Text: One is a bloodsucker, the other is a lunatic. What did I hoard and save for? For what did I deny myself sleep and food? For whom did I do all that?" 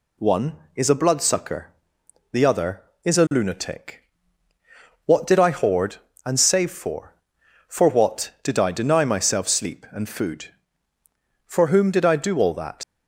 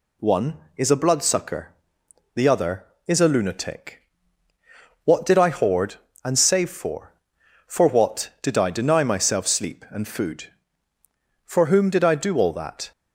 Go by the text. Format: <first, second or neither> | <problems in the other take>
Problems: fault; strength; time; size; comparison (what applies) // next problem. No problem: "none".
second | leaves "that" unfinished; at 12.8 s; 90 ms